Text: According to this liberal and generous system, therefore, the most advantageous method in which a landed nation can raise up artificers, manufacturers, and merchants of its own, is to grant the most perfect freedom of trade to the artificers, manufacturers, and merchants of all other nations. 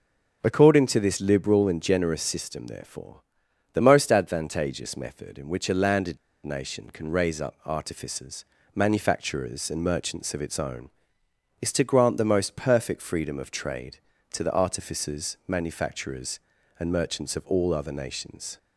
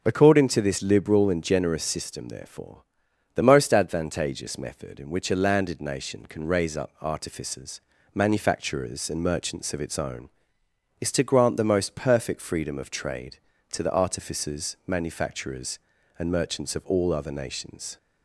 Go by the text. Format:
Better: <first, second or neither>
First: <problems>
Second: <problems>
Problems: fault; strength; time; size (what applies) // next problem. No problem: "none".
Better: second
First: starts louder than the rest; until 1.4 s; 6.5 dB // pauses between "landed" and "nation"; slight; at 6.1 s; 0.25 s long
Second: starts louder than the rest; until 1.0 s; 6.5 dB